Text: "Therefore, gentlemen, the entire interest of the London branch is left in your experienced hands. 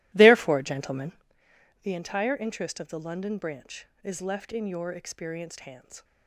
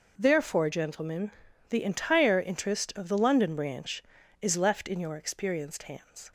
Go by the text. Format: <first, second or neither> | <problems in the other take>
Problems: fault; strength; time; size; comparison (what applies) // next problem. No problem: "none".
second | starts louder than the rest; strong; until 1.3 s; 16 dB